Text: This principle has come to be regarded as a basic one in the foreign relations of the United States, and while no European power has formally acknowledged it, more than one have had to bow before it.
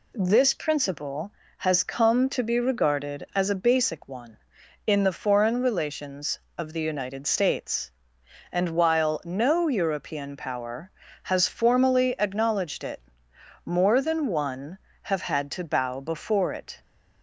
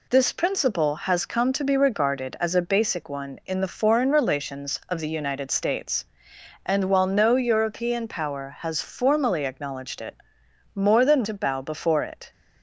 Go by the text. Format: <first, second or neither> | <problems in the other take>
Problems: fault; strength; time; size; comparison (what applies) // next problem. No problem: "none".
first | skips "one have had"; at 11.2 s